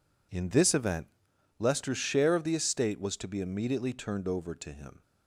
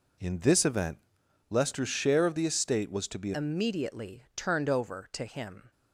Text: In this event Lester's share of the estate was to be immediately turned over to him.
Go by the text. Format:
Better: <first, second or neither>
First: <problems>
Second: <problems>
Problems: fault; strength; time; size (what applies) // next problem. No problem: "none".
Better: first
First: pauses between "event" and "Lester's"; noticeable; at 1.0 s; 0.52 s long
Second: pauses between "event" and "Lester's"; noticeable; at 0.9 s; 0.52 s long // changes voice at "immediately"; from 3.3 s on; 2.4 s long